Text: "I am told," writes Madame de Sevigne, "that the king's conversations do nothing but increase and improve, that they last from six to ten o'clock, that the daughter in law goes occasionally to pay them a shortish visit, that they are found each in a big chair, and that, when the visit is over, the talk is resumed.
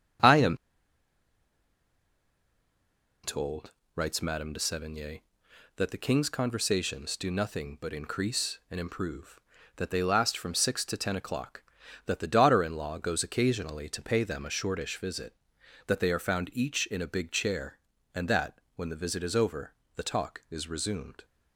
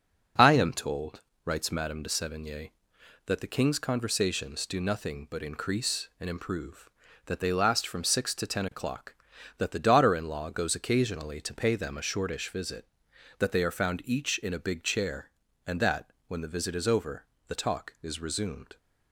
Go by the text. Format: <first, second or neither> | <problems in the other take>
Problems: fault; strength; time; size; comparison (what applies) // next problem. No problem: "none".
second | pauses between "am" and "told"; strong; at 0.5 s; 2.6 s long